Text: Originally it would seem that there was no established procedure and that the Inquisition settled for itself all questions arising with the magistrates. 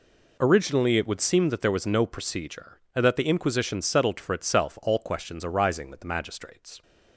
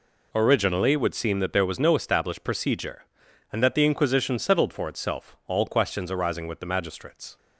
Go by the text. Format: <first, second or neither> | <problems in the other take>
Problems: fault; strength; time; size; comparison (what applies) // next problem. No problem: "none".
second | skips "established"; at 2.0 s